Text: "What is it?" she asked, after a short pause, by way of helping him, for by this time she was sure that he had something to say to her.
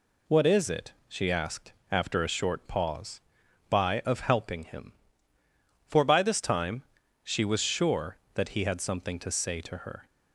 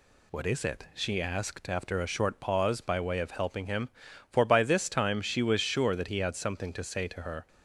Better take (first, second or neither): second